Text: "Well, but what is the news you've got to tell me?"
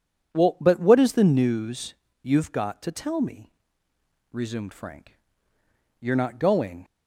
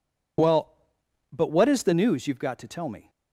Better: second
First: pauses between "news" and "you've"; slight; at 1.9 s; 0.28 s long // goes on to say "resumed Frank You're not going"; strong; from 4.3 s on; 2.5 s long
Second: none

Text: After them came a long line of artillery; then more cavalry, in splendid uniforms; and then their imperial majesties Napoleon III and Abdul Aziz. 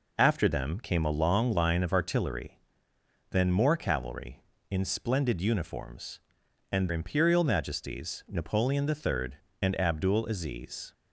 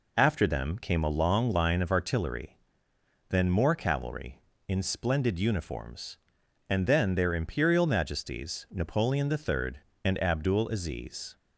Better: second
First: skips "then their"; at 6.8 s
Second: none

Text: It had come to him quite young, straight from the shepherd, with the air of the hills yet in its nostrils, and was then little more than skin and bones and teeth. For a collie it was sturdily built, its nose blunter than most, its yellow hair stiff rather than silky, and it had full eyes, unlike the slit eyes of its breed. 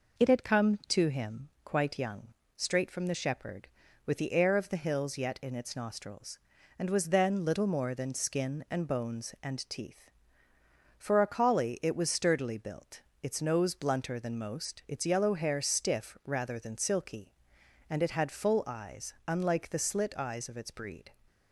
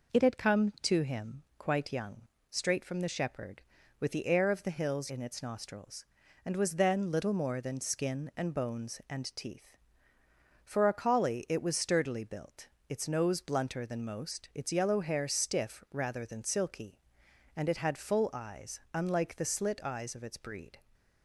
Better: first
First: none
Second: skips "yet"; at 5.0 s

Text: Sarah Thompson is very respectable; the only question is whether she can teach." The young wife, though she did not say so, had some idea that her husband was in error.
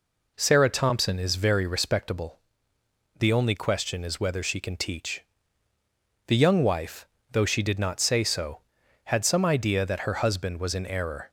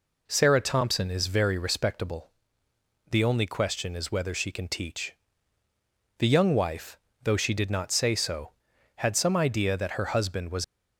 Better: first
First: none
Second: stops before "in error"; at 10.6 s

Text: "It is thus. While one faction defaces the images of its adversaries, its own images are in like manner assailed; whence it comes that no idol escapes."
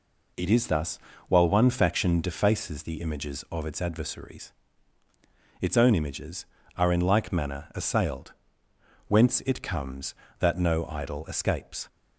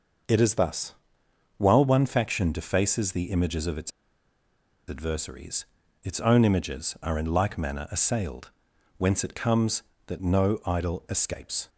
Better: first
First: none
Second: pauses between "its" and "adversaries"; noticeable; at 3.9 s; 0.97 s long

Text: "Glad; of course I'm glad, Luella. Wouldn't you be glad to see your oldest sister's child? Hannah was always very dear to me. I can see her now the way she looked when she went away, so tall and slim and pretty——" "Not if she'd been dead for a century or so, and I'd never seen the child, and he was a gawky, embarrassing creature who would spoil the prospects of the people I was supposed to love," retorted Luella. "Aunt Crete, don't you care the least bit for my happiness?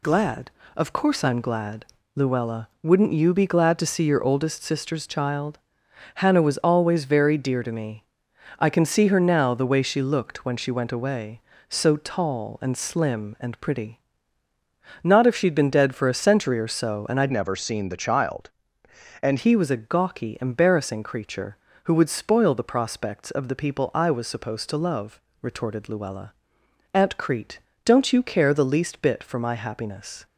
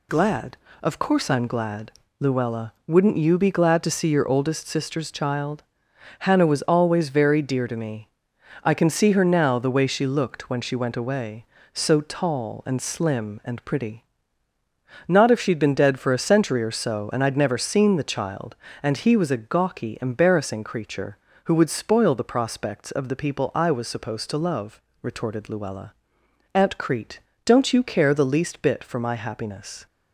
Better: second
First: changes voice from "never" to "and"; from 17.3 to 19.3 s; 2.0 s long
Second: none

